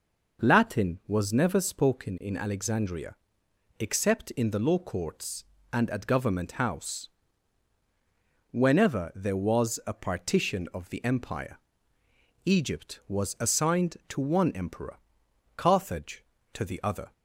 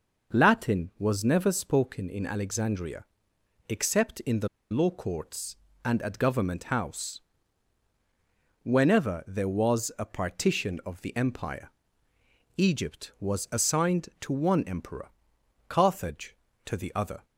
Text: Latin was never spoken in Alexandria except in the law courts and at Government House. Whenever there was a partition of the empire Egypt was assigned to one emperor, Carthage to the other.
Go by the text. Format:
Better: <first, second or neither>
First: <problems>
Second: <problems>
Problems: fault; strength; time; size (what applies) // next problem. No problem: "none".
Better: first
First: pauses between "Alexandria" and "except"; noticeable; at 3.1 s; 0.64 s long // pauses between "empire" and "Egypt"; noticeable; at 11.5 s; 0.86 s long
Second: pauses between "Alexandria" and "except"; noticeable; at 3.0 s; 0.64 s long // pauses between "the" and "law"; slight; at 4.4 s; 0.23 s long // pauses between "empire" and "Egypt"; noticeable; at 11.7 s; 0.86 s long